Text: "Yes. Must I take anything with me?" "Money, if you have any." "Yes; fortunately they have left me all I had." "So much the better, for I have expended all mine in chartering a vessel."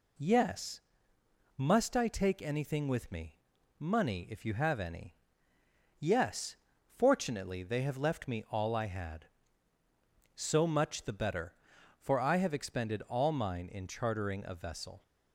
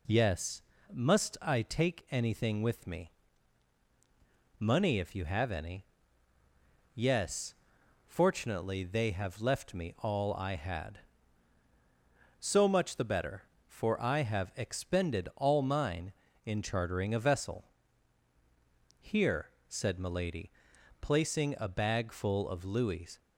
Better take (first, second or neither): first